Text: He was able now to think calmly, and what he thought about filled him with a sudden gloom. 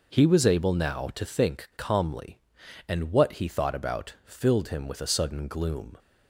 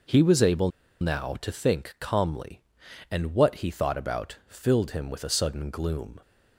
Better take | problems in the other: first | pauses between "able" and "now"; slight; at 0.6 s; 0.31 s long

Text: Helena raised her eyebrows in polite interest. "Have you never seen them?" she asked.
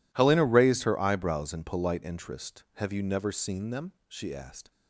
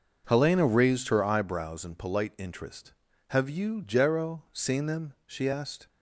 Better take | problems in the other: first | says "jero" for "never"; at 3.8 s

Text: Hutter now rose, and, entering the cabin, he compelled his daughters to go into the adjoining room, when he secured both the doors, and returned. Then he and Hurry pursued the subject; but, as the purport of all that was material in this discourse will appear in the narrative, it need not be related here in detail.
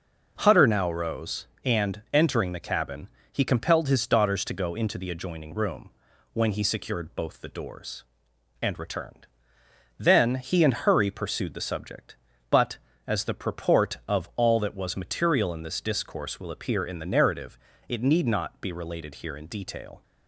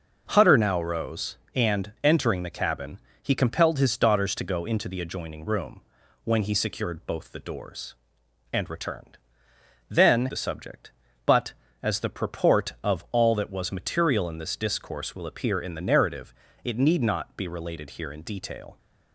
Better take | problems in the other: first | skips "he and Hurry pursued"; at 10.2 s

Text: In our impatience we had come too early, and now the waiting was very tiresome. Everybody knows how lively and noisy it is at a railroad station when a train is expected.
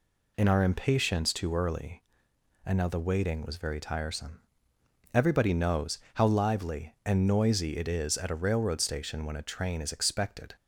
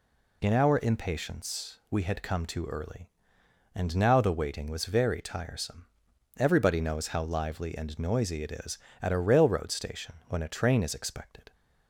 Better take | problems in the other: second | skips "we had come"; at 1.3 s // pauses between "knows" and "how"; slight; at 5.9 s; 0.16 s long

